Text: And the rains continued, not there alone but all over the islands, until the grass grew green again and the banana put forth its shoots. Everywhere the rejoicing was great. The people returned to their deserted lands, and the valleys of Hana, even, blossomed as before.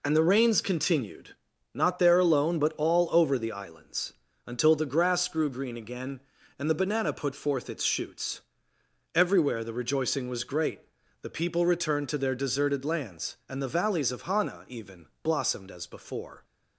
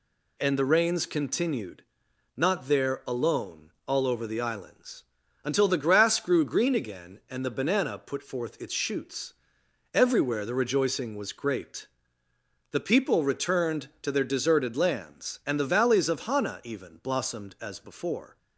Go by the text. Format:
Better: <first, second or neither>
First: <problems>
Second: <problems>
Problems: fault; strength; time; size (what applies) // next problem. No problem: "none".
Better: first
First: none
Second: skips "but"; at 3.7 s